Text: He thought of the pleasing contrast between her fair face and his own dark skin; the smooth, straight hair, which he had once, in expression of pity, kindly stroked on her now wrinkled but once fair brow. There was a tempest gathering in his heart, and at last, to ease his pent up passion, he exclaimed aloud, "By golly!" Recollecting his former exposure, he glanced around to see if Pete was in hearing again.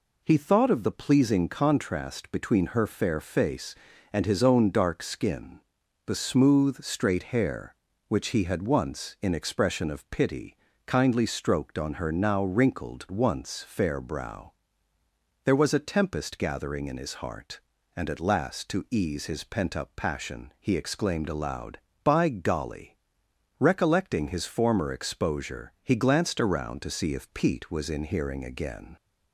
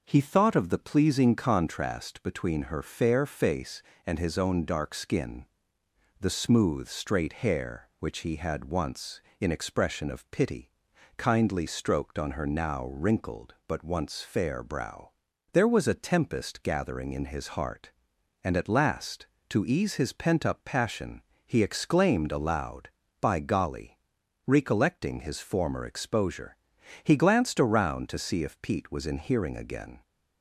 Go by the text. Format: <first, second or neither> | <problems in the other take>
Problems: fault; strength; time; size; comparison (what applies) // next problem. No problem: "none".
second | skips "but"; at 13.0 s